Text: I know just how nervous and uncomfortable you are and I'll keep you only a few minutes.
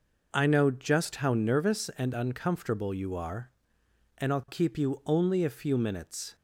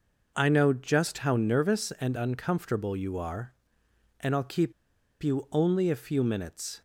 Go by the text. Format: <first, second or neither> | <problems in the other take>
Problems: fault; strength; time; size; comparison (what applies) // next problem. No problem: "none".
first | pauses between "keep" and "you"; noticeable; at 4.7 s; 0.50 s long